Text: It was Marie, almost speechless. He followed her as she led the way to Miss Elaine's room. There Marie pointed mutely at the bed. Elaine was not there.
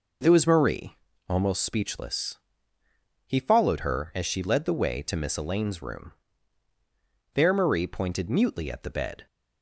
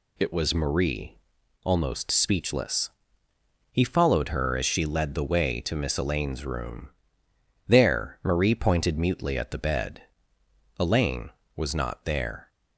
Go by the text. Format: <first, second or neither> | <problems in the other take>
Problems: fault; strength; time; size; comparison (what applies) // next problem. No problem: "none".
second | stops before "Elaine was not there"; at 9.2 s